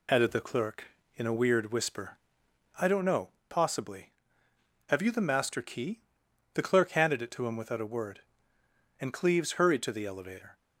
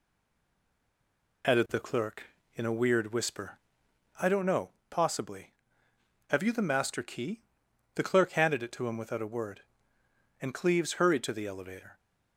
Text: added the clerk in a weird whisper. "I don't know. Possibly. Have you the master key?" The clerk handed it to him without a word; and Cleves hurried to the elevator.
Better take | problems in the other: first | stays silent before the first word; noticeable; until 1.4 s; 1.4 s long

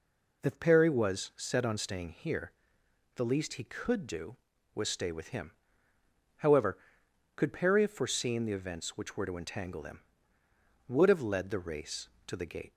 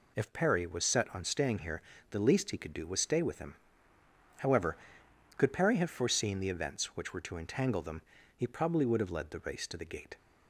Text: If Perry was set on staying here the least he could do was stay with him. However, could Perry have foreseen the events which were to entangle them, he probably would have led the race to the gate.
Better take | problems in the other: second | pauses between "here" and "the"; noticeable; at 2.5 s; 0.64 s long; slight in the second // skips "he probably"; at 10.4 s

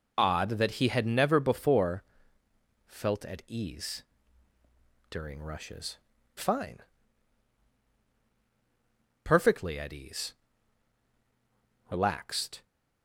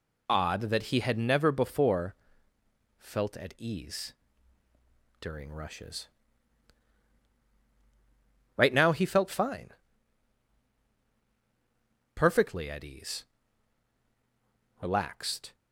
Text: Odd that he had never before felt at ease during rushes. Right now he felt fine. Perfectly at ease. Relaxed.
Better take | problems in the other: second | pauses between "before" and "felt"; noticeable; at 2.0 s; 0.82 s long; noticeable in the second // pauses between "ease" and "during"; at 4.0 s; 1.0 s long; also in the second // skips "Right now he felt"; at 6.1 s

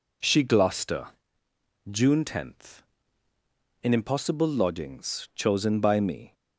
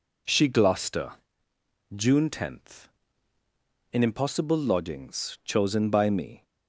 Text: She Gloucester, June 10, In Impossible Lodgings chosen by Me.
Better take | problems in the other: neither | none

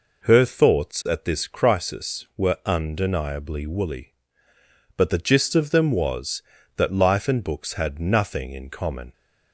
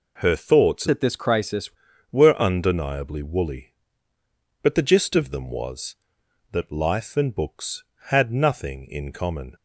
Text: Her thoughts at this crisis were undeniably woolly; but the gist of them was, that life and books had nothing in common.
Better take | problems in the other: first | changes voice from "at" to "crisis"; from 0.8 to 1.7 s; 0.9 s long

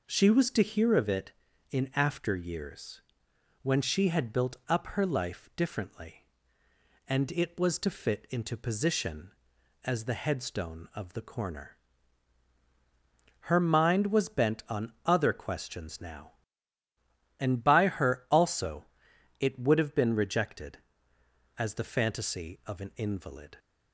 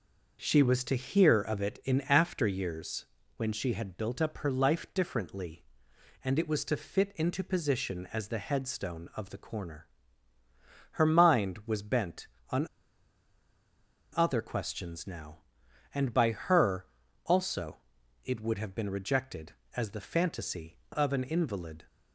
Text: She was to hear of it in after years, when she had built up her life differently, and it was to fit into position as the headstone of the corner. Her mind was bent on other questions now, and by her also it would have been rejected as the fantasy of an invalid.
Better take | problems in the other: first | pauses between "on" and "other"; strong; at 12.6 s; 1.4 s long // pauses between "her" and "also"; at 16.8 s; 0.40 s long // pauses between "also" and "it"; noticeable; at 17.7 s; 0.48 s long; noticeable in the first

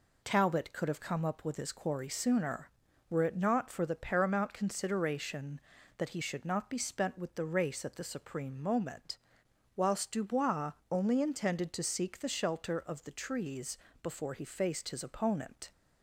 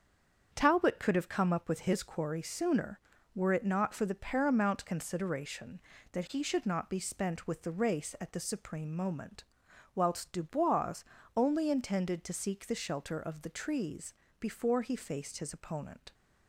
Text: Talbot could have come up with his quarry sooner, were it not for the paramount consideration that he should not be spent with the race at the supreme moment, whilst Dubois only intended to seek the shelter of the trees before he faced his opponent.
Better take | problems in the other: first | stays silent before the first word; slight; until 0.5 s; 0.5 s long // starts louder than the rest; strong; until 1.5 s; 7.5 dB // pauses between "Dubois" and "only"; slight; at 11.0 s; 0.34 s long; slight in the first // pauses between "trees" and "before"; slight; at 14.1 s; 0.26 s long; slight in the first

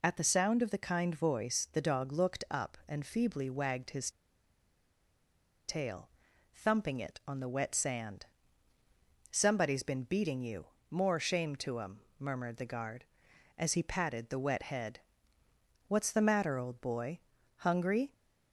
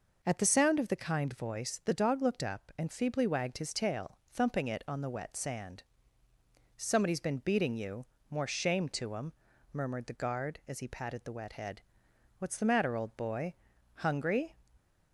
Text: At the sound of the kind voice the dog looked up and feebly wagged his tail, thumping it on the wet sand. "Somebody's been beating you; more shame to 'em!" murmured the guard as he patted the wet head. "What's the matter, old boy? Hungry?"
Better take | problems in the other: second | pauses between "his" and "tail"; strong; at 4.1 s; 1.5 s long

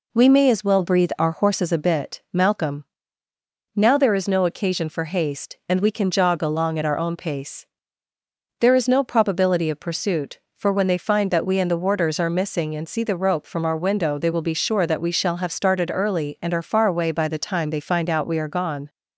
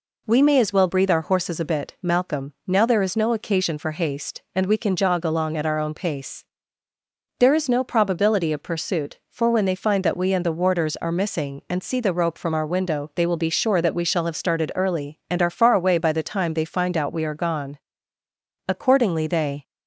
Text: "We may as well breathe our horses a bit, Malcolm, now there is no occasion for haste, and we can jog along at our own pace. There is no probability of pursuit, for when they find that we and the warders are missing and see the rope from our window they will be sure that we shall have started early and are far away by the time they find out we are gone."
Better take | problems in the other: first | goes on to say "Accordingly they"; noticeable; from 18.6 s on; 0.96 s long

